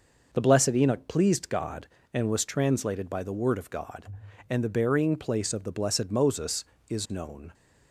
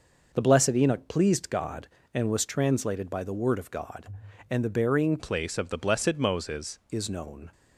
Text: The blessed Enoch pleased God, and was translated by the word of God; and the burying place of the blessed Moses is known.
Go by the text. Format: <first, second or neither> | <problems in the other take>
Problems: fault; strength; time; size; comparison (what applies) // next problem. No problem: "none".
first | changes voice from "place" to "Moses"; from 5.1 to 6.7 s; 1.6 s long